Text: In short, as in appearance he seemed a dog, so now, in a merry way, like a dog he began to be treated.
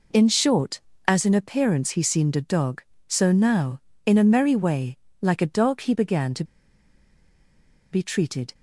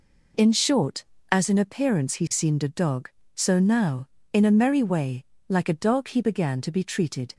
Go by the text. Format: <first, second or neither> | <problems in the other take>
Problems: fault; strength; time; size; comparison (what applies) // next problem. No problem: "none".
second | pauses between "to" and "be"; strong; at 6.4 s; 1.4 s long